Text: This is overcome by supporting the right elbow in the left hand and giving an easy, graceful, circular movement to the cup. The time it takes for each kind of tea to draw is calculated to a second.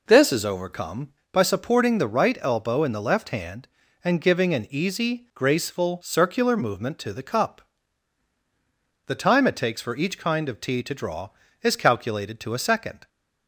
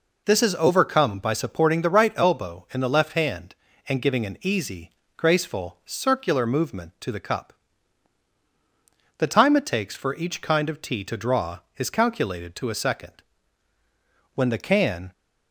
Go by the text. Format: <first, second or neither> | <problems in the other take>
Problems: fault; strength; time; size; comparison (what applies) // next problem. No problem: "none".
first | goes on to say "When the can"; noticeable; from 14.3 s on; 0.78 s long